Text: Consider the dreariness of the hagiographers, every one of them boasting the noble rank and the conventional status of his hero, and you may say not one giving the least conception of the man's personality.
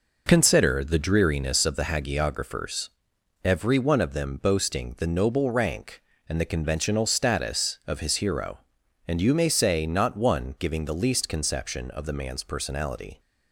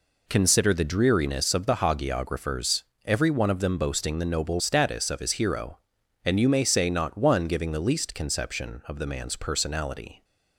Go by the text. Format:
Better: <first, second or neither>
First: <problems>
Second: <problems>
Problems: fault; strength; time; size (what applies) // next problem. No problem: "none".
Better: first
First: none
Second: skips "rank and the conventional"; at 4.5 s